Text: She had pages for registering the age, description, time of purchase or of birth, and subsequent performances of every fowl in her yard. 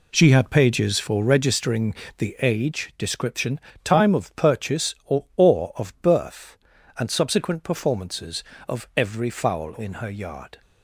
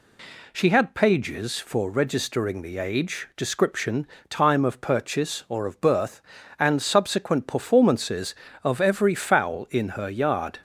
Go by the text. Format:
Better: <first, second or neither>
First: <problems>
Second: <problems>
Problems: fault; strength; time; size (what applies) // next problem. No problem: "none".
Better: second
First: pauses between "registering" and "the"; slight; at 1.9 s; 0.24 s long // says "or" twice; at 5.3 s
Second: none